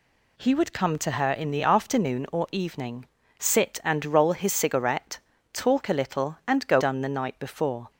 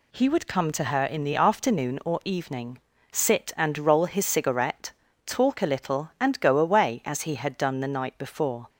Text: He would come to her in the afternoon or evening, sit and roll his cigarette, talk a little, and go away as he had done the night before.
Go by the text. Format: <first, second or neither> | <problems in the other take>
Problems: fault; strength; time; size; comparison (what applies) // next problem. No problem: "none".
second | skips "away as he had"; at 6.8 s